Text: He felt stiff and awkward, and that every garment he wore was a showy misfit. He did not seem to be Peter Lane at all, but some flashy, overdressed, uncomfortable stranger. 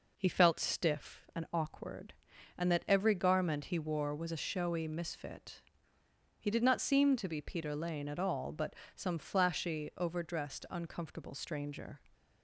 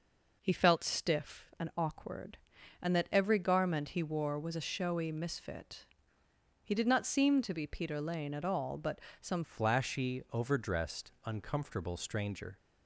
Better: first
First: pauses between "but" and "some"; slight; at 8.7 s; 0.20 s long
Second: pauses between "but" and "some"; slight; at 9.0 s; 0.20 s long // changes voice at "flashy"; from 9.4 s on; 3.1 s long

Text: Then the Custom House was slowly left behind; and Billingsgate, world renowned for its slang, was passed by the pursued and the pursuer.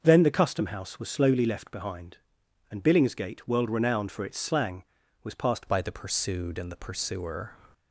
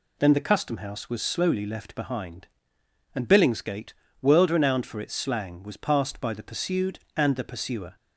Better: second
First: starts louder than the rest; until 1.0 s; 6.5 dB // changes voice at "by"; from 5.6 s on; 1.9 s long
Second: none

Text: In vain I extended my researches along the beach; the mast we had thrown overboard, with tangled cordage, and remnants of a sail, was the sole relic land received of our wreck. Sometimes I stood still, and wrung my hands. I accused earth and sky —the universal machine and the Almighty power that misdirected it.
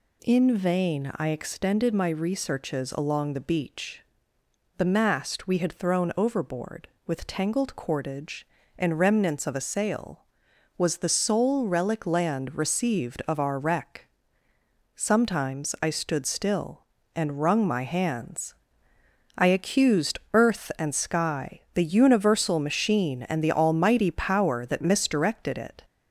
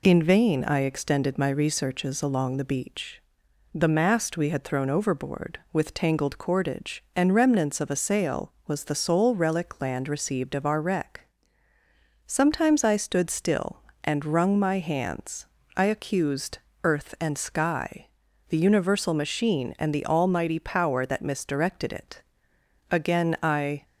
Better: first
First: none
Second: pauses between "accused" and "earth"; slight; at 16.5 s; 0.24 s long // goes on to say "Again I"; noticeable; from 22.9 s on; 0.94 s long

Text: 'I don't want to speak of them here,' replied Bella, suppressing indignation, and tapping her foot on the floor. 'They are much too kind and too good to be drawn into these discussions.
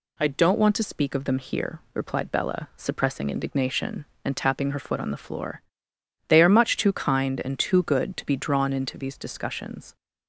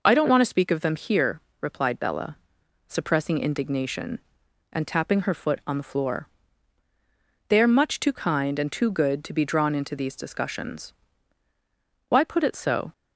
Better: first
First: none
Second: goes on to say "Why put it so"; noticeable; from 12.0 s on; 0.84 s long

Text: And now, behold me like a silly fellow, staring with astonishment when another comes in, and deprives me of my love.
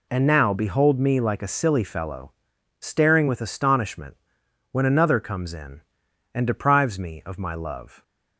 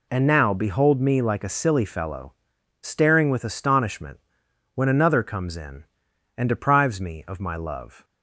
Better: neither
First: pauses between "astonishment" and "when"; noticeable; at 4.1 s; 0.56 s long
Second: pauses between "astonishment" and "when"; noticeable; at 4.1 s; 0.56 s long

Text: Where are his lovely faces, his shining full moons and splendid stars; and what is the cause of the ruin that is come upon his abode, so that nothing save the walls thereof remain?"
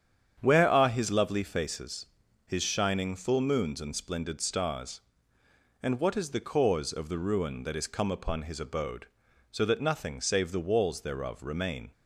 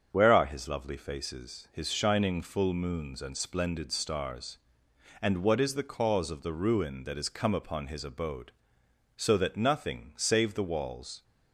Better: first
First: starts louder than the rest; strong; until 1.4 s; 8.5 dB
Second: starts louder than the rest; until 1.1 s; 7 dB // stops before "thereof remain"; at 11.2 s

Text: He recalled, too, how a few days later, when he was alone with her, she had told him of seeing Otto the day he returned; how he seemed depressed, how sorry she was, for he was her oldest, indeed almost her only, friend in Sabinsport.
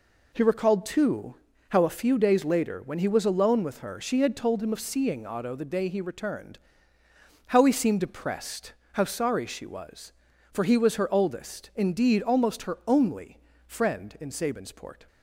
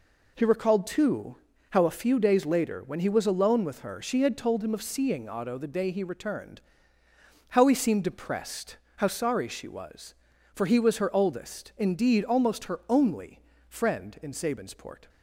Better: neither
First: none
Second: none

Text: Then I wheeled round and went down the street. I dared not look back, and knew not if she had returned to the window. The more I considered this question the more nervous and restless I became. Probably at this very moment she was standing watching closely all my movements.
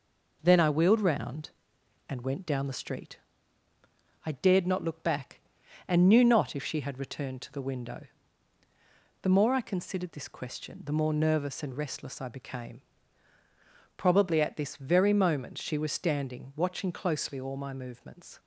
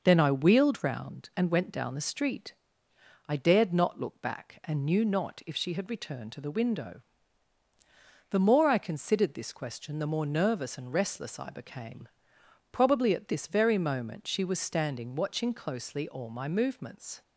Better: neither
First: none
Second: none

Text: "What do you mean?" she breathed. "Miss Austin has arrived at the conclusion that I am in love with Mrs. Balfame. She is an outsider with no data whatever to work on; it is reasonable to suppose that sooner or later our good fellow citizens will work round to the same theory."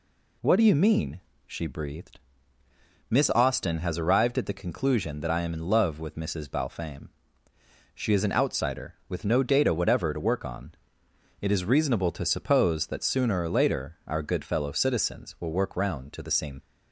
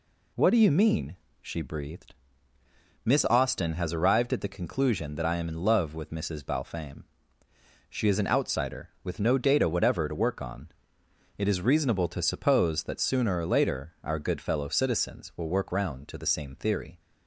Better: second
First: stops before "theory"; at 16.6 s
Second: none

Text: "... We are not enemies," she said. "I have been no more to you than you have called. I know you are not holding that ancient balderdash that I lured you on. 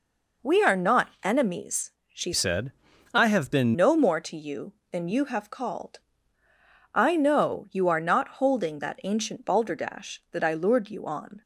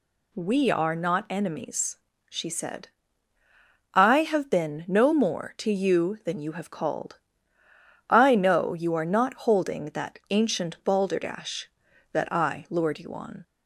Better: second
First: changes voice from "said" to "been"; from 2.3 to 3.7 s; 1.4 s long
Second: none

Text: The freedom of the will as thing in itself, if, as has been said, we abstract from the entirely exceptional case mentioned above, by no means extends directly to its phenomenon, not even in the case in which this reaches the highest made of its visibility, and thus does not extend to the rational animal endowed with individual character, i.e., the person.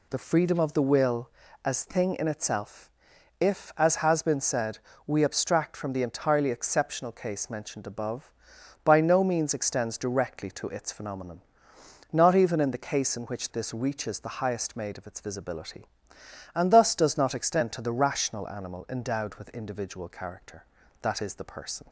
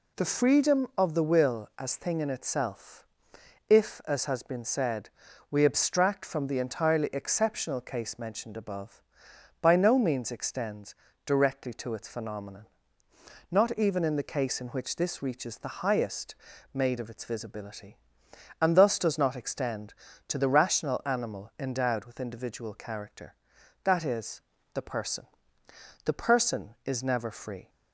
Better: first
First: none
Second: pauses between "extends" and "directly"; slight; at 10.9 s; 0.32 s long // pauses between "highest" and "made"; slight; at 16.3 s; 0.36 s long // goes on to say "The person is never free"; from 26.0 s on; 1.6 s long

